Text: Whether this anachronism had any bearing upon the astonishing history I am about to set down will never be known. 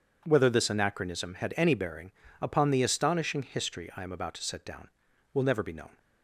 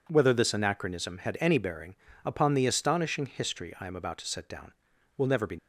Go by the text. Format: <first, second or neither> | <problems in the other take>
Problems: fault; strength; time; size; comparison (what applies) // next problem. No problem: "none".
first | pauses between "bearing" and "upon"; slight; at 1.9 s; 0.30 s long; slight in the first // stops before "known"; at 5.5 s